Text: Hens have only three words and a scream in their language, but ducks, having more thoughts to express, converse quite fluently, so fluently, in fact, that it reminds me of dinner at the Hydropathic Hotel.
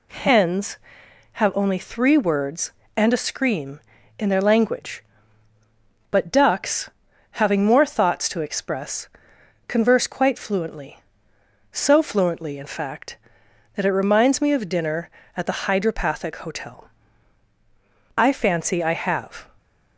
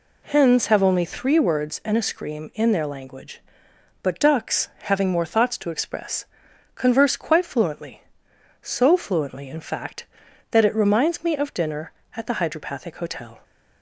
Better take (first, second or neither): second